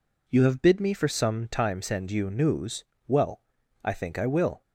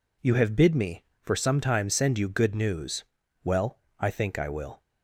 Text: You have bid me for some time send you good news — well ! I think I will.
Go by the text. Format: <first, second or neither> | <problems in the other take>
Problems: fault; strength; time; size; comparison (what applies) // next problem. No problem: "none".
second | skips "good"; at 2.3 s